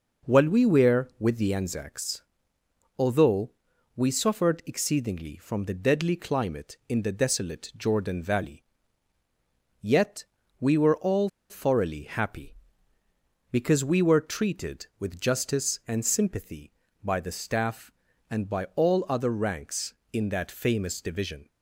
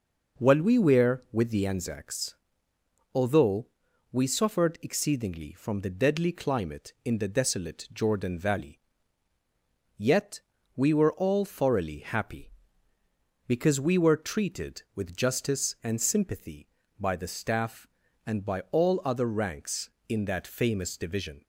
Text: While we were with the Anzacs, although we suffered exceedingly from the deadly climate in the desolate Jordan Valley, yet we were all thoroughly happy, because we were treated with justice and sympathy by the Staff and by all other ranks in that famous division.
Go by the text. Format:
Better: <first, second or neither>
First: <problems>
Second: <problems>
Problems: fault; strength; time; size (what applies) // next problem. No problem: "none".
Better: second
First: pauses between "although" and "we"; noticeable; at 3.5 s; 0.46 s long // pauses between "yet" and "we"; at 10.2 s; 0.38 s long // pauses between "all" and "thoroughly"; slight; at 11.2 s; 0.23 s long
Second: pauses between "although" and "we"; noticeable; at 3.6 s; 0.46 s long // pauses between "yet" and "we"; at 10.3 s; 0.38 s long